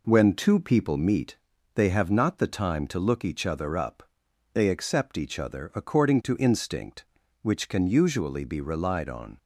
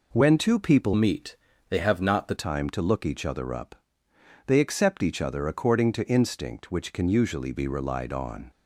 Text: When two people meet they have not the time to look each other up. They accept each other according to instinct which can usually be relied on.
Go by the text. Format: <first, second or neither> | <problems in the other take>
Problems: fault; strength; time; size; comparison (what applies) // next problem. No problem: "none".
first | changes voice from "meet" to "the"; from 0.9 to 2.3 s; 1.4 s long // pauses between "meet" and "they"; slight; at 1.3 s; 0.36 s long; also in the first